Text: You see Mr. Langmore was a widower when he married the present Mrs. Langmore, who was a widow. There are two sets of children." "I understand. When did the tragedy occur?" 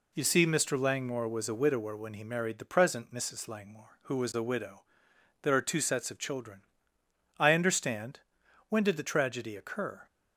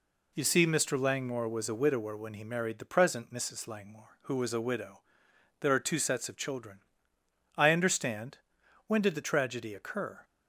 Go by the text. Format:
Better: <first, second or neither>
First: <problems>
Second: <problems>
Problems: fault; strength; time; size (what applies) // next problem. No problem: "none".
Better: neither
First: none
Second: none